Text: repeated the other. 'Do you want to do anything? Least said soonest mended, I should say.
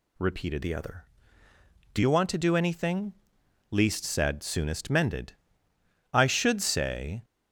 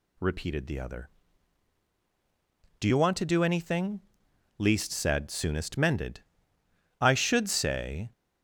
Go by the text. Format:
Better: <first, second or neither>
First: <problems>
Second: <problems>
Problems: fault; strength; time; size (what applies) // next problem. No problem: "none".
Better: second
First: changes voice from "the" to "Do"; from 0.6 to 1.9 s; 1.3 s long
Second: none